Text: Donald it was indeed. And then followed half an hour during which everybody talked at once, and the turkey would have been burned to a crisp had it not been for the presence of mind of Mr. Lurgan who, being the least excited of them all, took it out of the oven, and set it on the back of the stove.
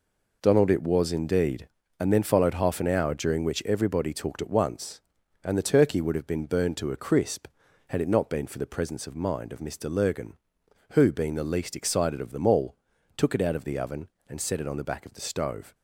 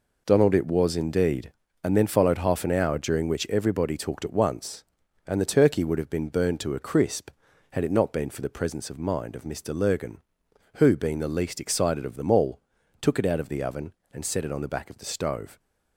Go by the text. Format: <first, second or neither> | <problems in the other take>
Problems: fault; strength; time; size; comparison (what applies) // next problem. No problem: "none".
neither | none